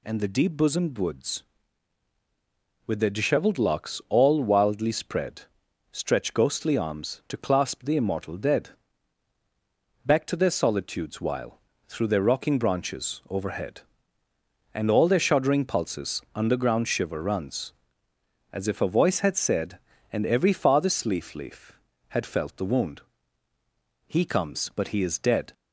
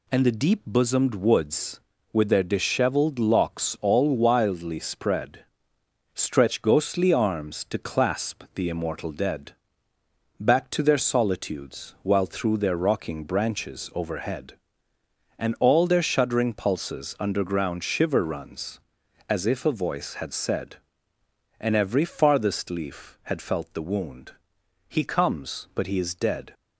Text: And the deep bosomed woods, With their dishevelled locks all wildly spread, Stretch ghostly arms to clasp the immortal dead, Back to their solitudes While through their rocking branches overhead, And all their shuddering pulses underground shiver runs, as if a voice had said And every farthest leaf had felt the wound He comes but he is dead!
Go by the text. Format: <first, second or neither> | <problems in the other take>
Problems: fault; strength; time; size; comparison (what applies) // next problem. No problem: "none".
second | pauses between "While" and "through"; slight; at 11.5 s; 0.28 s long // says "leaf" twice; at 21.3 s // pauses between "wound" and "He"; at 23.0 s; 1.0 s long; noticeable in the second